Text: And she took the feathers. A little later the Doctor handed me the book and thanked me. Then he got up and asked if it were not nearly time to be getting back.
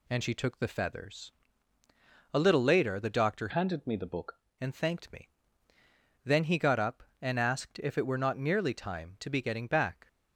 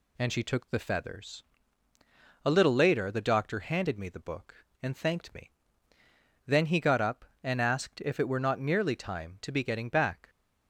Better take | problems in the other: second | changes voice from "handed" to "book"; from 3.5 to 4.4 s; 0.9 s long

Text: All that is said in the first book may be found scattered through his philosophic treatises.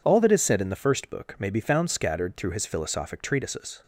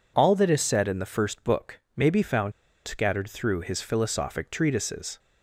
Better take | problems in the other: first | pauses between "book" and "may"; slight; at 1.7 s; 0.16 s long // pauses between "found" and "scattered"; slight; at 2.5 s; 0.34 s long

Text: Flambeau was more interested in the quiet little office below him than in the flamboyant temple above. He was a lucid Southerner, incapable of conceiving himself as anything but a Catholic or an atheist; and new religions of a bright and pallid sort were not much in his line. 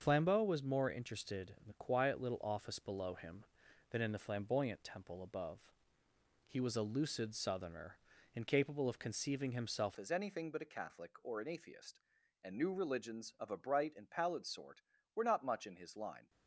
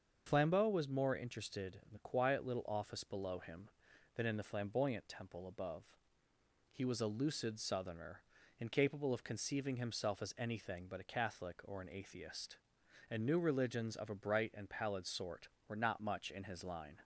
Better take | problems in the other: second | starts louder than the rest; until 1.0 s; 6.5 dB; also in the second // changes voice at "as"; from 9.9 s on; 6.3 s long

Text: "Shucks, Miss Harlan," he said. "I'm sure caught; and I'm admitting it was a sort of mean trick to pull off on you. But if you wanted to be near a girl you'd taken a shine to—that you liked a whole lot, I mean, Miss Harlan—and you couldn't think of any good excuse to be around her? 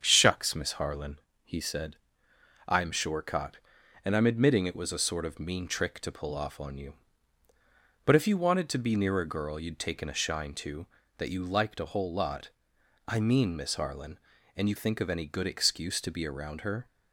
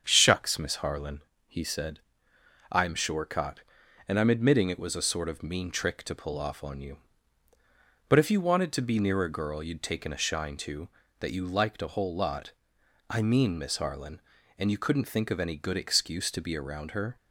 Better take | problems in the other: second | starts louder than the rest; strong; until 1.0 s; 7.5 dB; strong in the second // skips "couldn't"; at 14.7 s

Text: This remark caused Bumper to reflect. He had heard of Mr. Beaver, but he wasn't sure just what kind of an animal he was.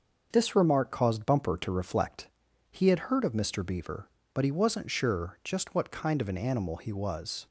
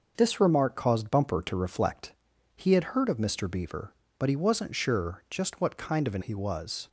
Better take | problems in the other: first | starts louder than the rest; noticeable; until 1.1 s; 6 dB; also in the first // skips "animal"; at 6.2 s

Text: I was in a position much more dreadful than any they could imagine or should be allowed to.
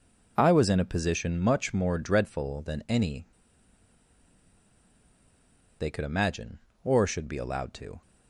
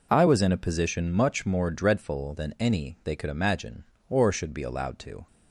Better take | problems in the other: second | pauses between "any" and "they"; strong; at 3.2 s; 2.5 s long

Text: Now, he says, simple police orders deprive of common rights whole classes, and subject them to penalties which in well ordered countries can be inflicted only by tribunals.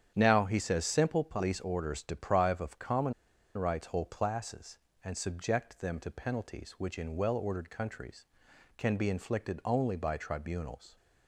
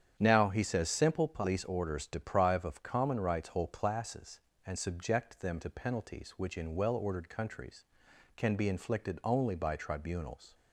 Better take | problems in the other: second | starts louder than the rest; strong; until 1.1 s; 8.5 dB; strong in the second // pauses between "common" and "rights"; at 3.1 s; 0.44 s long

